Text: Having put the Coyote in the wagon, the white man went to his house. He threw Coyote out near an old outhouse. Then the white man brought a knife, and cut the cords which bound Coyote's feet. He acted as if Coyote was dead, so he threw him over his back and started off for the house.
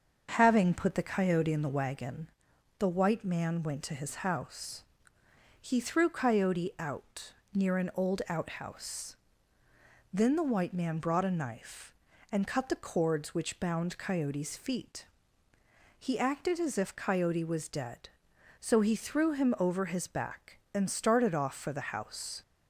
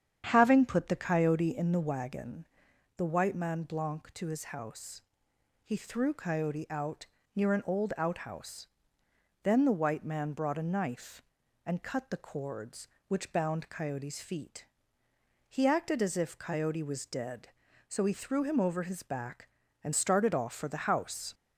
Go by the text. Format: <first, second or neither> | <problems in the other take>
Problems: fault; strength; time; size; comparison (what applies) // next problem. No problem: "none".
first | starts louder than the rest; strong; until 1.2 s; 8.5 dB; also in the first // says "blanc" for "went"; at 3.6 s // pauses between "out" and "near"; slight; at 7.0 s; 0.30 s long; slight in the first